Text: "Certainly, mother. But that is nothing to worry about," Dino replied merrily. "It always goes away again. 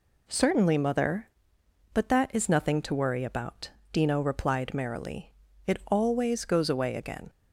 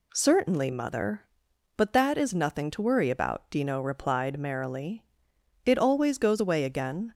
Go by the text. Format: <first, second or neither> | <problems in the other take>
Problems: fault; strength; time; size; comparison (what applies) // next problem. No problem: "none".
neither | none